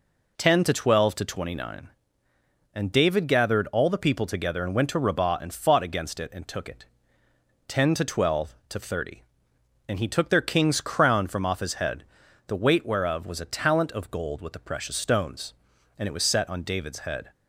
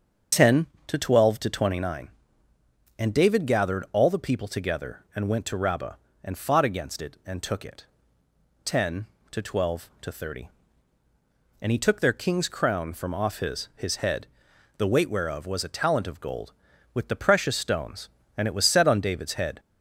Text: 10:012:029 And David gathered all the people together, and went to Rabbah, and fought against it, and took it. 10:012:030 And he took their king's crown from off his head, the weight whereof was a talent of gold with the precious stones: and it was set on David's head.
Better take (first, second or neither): first